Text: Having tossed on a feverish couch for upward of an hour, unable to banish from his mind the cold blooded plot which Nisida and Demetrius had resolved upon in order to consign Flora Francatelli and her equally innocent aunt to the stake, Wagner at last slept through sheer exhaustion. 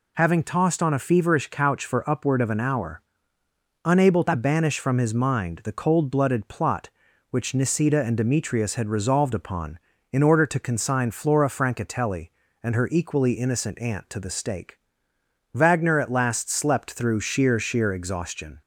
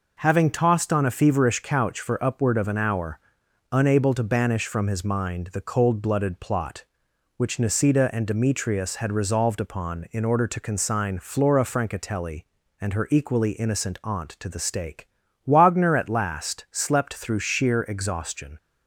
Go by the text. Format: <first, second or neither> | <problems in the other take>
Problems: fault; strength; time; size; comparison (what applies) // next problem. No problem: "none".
second | says "sheer" twice; at 17.5 s